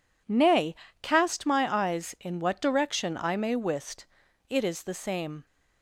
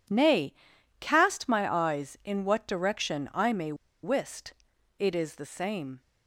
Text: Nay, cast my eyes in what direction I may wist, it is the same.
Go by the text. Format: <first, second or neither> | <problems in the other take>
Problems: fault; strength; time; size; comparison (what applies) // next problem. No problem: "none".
first | pauses between "may" and "wist"; slight; at 3.7 s; 0.29 s long